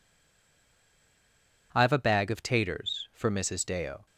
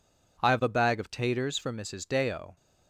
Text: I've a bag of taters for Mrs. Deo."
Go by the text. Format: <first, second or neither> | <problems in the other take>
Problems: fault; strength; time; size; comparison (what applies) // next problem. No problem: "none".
second | stays silent before the first word; noticeable; until 1.7 s; 1.7 s long